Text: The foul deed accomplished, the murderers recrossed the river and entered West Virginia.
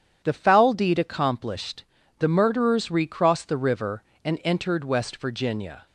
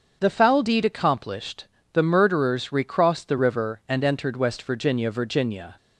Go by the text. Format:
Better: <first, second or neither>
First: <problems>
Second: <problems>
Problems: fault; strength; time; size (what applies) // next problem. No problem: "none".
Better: first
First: none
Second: starts louder than the rest; until 1.2 s; 7 dB // says "Virginia" twice; at 5.1 s